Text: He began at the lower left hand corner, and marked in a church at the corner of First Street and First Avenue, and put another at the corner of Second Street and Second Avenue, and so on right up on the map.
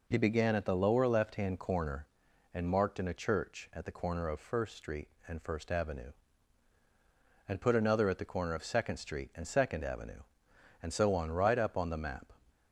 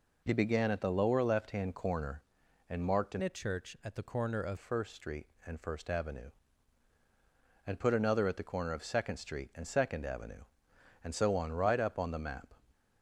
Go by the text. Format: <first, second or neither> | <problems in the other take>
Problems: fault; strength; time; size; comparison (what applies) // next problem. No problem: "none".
first | changes voice from "a" to "of"; from 3.2 to 4.5 s; 1.3 s long